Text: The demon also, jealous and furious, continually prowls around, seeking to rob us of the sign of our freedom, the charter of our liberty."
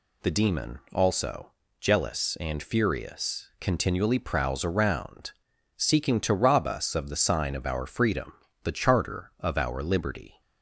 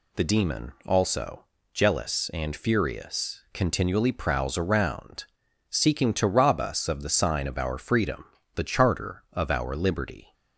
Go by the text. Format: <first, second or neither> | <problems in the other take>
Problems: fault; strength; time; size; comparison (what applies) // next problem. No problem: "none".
neither | none